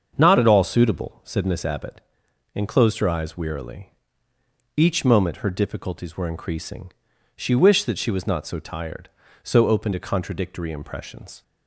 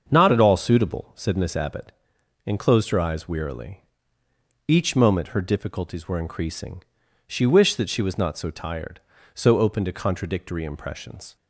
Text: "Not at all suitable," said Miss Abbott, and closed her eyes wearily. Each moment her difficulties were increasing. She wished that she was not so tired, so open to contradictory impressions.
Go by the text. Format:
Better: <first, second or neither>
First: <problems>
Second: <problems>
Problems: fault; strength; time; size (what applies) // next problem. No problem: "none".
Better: neither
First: starts louder than the rest; until 1.1 s; 7 dB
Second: starts louder than the rest; until 1.0 s; 7 dB